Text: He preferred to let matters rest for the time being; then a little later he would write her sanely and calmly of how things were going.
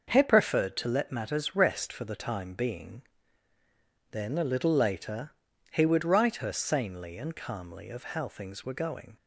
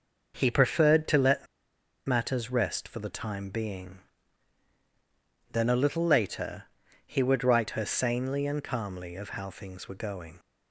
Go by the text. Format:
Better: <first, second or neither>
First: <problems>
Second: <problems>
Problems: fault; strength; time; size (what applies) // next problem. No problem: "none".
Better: first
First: starts louder than the rest; until 1.1 s; 6 dB // pauses between "later" and "he"; at 5.3 s; 0.40 s long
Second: starts louder than the rest; noticeable; until 1.3 s; 6 dB // pauses between "let" and "matters"; noticeable; at 1.4 s; 0.61 s long // pauses between "later" and "he"; at 6.6 s; 0.42 s long